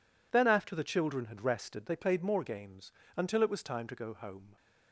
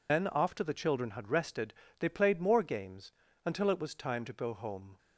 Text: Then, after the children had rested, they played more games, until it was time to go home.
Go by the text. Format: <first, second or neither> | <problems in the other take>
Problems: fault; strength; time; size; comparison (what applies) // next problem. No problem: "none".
first | loses the start of "Then"; at 0.0 s; 110 ms